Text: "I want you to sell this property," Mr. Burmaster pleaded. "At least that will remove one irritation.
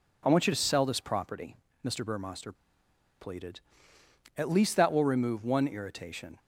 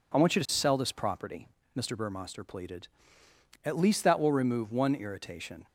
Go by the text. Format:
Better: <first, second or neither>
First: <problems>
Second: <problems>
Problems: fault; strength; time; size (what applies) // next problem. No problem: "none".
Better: second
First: pauses between "Burmaster" and "pleaded"; noticeable; at 2.5 s; 0.66 s long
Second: none